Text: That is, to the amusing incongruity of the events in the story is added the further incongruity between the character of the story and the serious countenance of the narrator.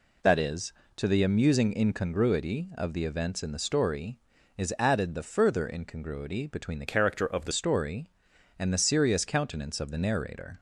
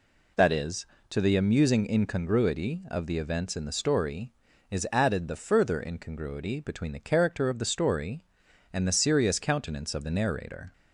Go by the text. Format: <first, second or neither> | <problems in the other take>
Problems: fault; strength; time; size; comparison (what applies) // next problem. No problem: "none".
second | changes voice from "character" to "the"; from 6.8 to 7.5 s; 0.7 s long